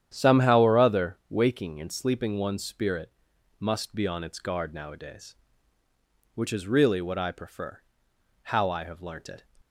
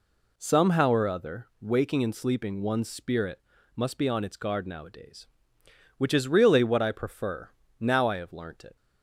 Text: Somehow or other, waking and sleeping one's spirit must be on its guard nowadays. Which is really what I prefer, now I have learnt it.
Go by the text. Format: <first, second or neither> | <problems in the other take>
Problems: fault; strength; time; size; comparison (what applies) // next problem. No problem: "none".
second | starts louder than the rest; strong; until 1.1 s; 10 dB // pauses between "spirit" and "must"; noticeable; at 3.1 s; 0.48 s long; slight in the second // says "how" for "now"; at 8.4 s